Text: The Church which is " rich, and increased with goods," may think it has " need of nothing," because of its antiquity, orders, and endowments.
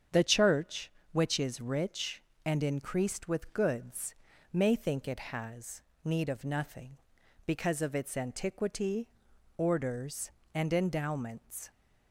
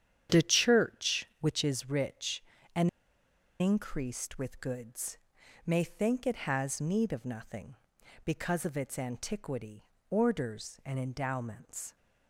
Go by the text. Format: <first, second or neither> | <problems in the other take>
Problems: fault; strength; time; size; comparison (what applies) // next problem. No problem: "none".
first | starts louder than the rest; strong; until 1.4 s; 9 dB; strong in the first // pauses between "and" and "increased"; noticeable; at 2.8 s; 0.71 s long